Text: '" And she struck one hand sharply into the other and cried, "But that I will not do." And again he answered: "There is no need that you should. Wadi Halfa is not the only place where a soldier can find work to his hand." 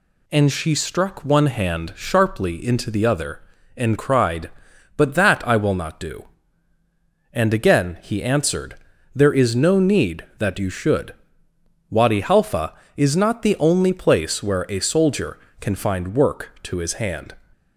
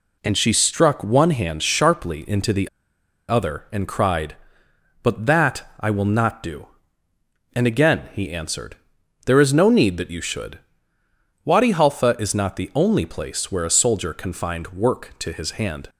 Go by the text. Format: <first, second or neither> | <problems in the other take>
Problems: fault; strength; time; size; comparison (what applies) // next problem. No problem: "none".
first | pauses between "the" and "other"; noticeable; at 2.6 s; 0.61 s long